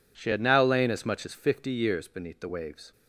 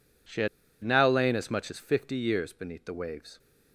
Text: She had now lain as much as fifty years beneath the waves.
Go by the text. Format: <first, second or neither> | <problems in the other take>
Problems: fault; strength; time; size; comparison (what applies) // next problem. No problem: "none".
first | pauses between "had" and "now"; at 0.4 s; 0.36 s long